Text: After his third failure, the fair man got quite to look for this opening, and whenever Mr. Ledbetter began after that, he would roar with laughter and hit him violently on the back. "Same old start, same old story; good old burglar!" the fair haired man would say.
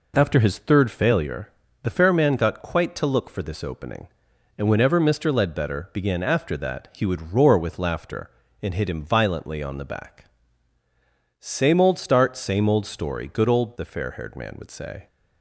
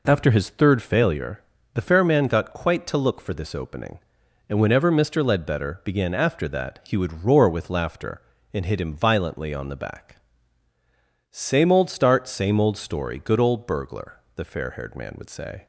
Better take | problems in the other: second | skips "burglar"; at 13.7 s

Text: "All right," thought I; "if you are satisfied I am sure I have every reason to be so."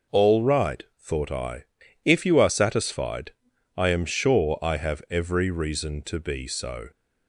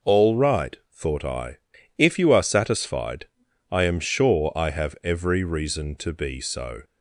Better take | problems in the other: neither | pauses between "satisfied" and "I"; the same in both

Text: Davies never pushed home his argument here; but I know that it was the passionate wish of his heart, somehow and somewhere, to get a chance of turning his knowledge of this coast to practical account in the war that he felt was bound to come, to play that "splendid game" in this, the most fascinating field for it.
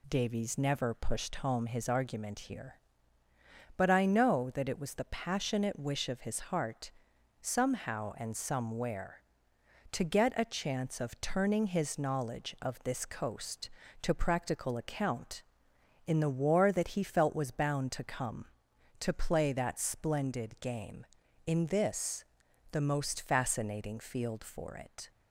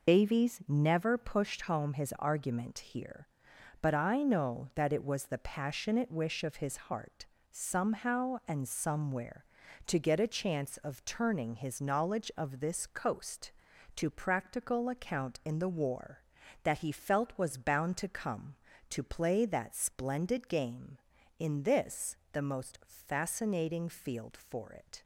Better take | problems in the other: first | loses the start of "Davies"; at 0.0 s; 65 ms

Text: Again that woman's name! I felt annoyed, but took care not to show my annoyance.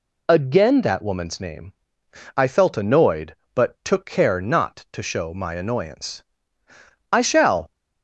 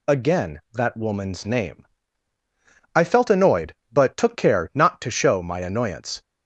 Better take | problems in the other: second | goes on to say "I shall"; from 7.1 s on; 0.60 s long

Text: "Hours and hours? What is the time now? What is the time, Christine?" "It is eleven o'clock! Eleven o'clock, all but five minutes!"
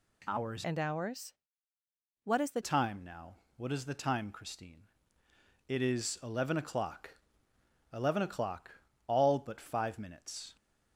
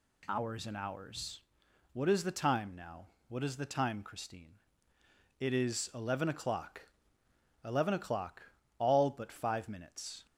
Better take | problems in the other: second | changes voice from "and" to "the"; from 0.6 to 2.6 s; 2.0 s long

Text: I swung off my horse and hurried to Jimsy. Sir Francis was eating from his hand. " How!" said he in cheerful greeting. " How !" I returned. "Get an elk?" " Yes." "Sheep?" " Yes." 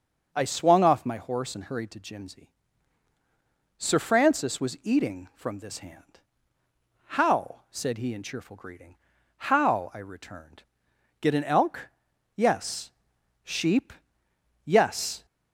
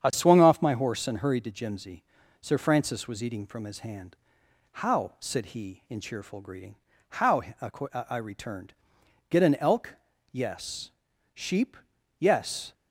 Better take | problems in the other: second | starts louder than the rest; strong; until 1.3 s; 7 dB; strong in the second // says "this" for "his"; at 5.5 s

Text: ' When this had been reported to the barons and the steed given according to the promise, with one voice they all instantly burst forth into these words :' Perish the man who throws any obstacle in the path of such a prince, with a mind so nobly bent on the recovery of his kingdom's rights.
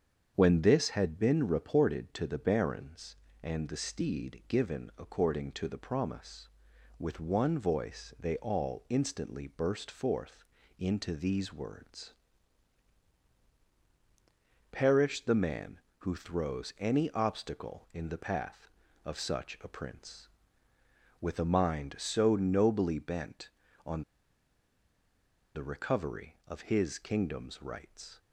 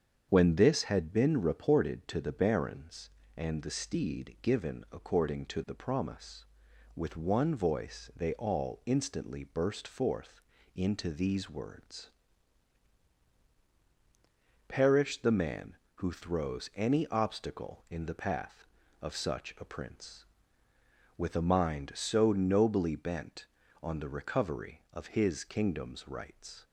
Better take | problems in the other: second | starts louder than the rest; strong; until 1.3 s; 7.5 dB; strong in the second // pauses between "forth" and "into"; slight; at 10.4 s; 0.34 s long; slight in the second // pauses between "on" and "the"; strong; at 24.0 s; 1.5 s long

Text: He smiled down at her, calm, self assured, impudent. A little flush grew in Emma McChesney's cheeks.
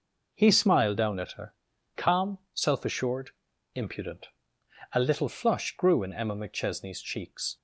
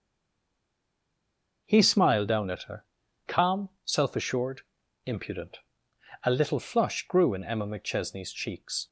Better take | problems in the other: first | stays silent before the first word; noticeable; until 1.6 s; 1.6 s long

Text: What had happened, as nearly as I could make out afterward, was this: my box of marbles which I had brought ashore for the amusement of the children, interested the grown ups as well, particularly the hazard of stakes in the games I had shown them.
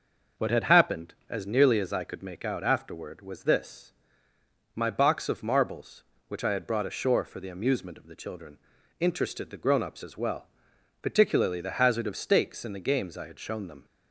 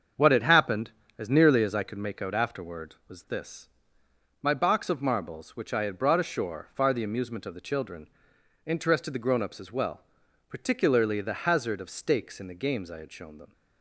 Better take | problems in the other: first | starts louder than the rest; until 1.4 s; 7 dB; noticeable in the first // says "far" for "for"; at 6.7 s

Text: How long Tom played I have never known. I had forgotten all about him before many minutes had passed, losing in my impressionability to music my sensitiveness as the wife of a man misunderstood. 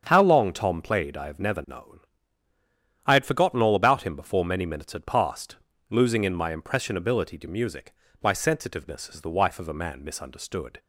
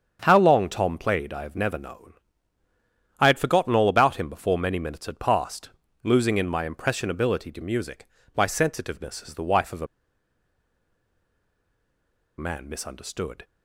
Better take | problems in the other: first | starts louder than the rest; strong; until 1.2 s; 7.5 dB; strong in the first // pauses between "music" and "my"; slight; at 8.0 s; 0.30 s long; slight in the first // pauses between "a" and "man"; strong; at 9.8 s; 2.5 s long

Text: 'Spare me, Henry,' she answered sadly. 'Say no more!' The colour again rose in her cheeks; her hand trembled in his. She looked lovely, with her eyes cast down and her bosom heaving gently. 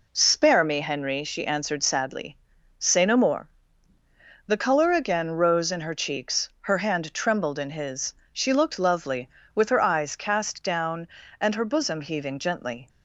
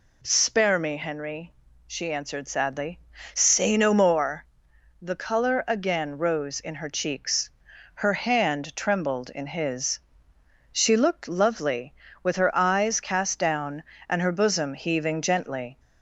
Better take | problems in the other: neither | none

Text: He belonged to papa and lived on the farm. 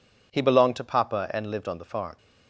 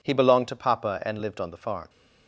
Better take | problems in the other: neither | none

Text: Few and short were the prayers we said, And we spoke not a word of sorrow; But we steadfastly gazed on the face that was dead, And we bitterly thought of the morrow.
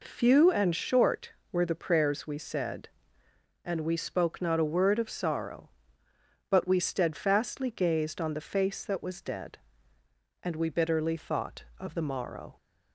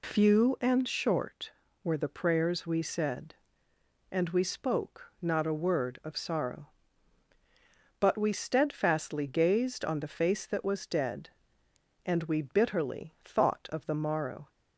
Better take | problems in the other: neither | none

